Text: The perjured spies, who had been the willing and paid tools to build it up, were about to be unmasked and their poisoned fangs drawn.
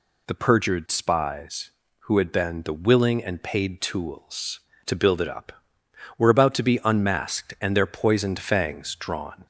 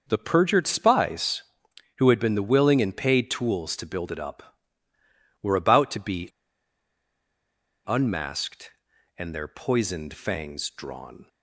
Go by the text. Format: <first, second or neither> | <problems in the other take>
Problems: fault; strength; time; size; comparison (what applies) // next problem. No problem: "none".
first | starts louder than the rest; noticeable; until 1.0 s; 6 dB // pauses between "be" and "unmasked"; strong; at 6.2 s; 1.5 s long